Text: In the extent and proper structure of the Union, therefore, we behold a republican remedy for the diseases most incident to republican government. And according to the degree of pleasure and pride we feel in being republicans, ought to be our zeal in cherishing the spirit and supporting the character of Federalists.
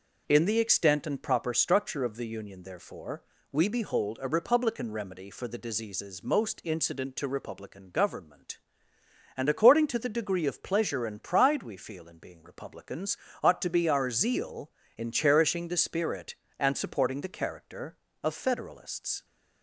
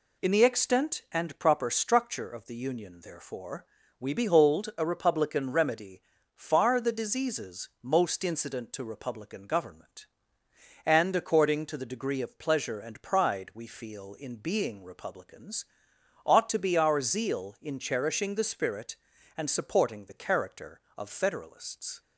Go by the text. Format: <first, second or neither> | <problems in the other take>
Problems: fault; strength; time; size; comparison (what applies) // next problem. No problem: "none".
first | says "far" for "for"; at 6.3 s